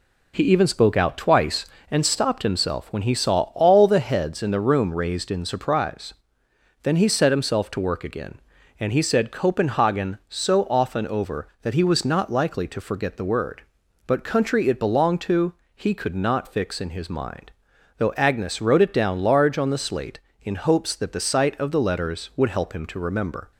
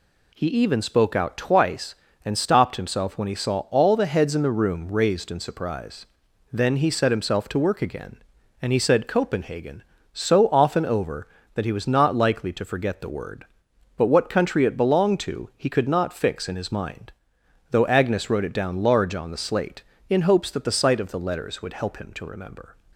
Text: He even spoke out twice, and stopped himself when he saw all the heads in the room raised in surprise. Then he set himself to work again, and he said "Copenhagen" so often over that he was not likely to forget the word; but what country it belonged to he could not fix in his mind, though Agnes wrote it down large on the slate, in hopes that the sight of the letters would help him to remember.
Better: second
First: skips "what"; at 14.2 s // pauses between "to" and "he"; slight; at 15.5 s; 0.22 s long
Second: none

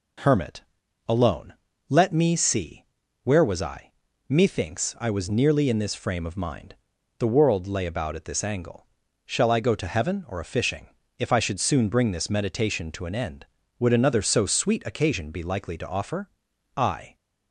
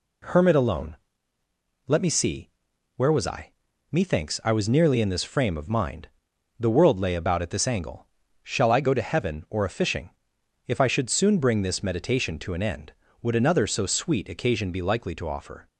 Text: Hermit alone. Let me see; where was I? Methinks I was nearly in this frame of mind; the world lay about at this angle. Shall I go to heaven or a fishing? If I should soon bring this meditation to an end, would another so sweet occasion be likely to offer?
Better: second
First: pauses between "Hermit" and "alone"; at 0.6 s; 0.44 s long // goes on to say "I"; slight; from 16.7 s on; 0.38 s long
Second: none

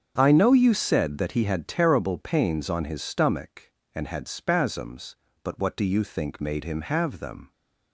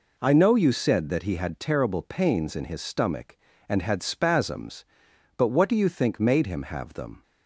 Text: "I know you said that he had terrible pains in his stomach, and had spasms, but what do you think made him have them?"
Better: second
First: starts louder than the rest; until 1.1 s; 7 dB // says "on" for "in"; at 2.6 s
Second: none

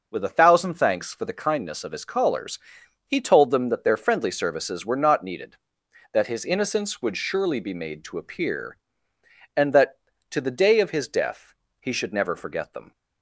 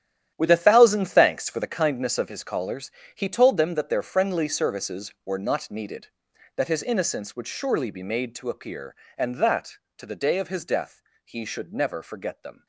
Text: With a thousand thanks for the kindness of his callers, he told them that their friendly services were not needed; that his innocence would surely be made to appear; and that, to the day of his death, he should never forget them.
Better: first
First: none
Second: gets quieter; strong; throughout; 13 dB

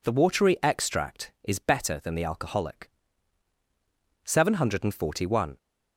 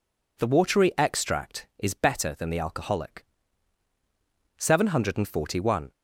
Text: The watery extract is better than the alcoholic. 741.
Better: neither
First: none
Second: none

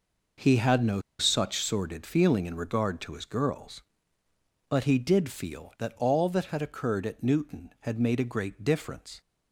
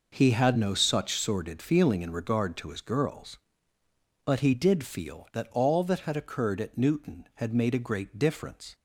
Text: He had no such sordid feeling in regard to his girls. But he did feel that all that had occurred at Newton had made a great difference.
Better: second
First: pauses between "no" and "such"; slight; at 1.0 s; 0.18 s long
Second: none

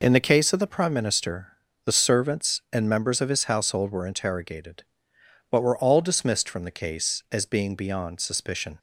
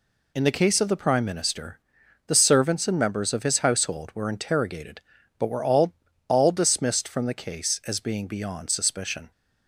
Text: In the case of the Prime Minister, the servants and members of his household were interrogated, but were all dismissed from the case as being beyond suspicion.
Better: first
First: none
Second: says "all" twice; at 6.2 s

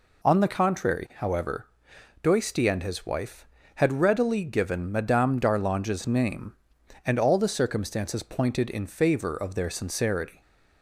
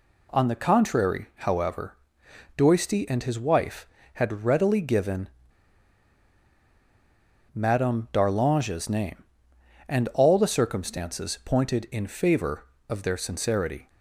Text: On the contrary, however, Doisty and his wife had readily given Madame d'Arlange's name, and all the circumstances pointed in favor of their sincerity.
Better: first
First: none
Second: pauses between "given" and "Madame"; strong; at 5.2 s; 2.2 s long

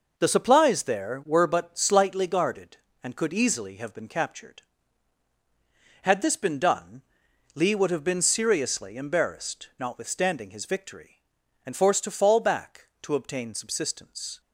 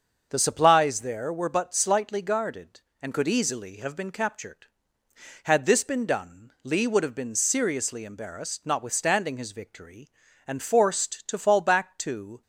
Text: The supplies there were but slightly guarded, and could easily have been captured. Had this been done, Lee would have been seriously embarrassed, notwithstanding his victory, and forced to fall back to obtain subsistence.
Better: first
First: none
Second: starts louder than the rest; until 1.3 s; 6.5 dB // stops before "obtain subsistence"; at 12.4 s

